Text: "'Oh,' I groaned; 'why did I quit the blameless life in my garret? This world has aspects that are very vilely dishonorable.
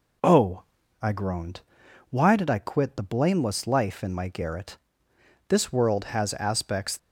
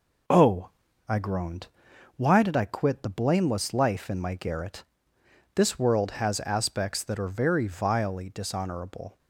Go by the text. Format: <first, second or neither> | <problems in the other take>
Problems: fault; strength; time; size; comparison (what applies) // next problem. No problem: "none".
second | stops before "that are very vilely dishonorable"; at 6.9 s